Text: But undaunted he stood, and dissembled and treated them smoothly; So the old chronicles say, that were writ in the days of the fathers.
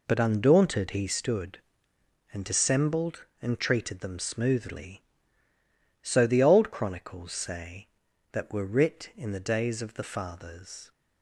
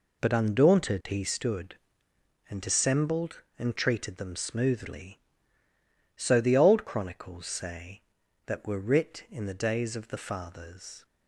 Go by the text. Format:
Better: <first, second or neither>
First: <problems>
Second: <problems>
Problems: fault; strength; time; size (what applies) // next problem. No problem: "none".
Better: neither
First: none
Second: none